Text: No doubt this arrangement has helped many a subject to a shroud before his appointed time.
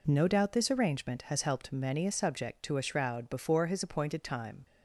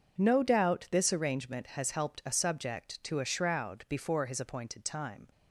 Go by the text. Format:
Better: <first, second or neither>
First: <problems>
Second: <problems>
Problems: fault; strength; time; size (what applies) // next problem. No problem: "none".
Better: first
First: none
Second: skips "many"; at 2.2 s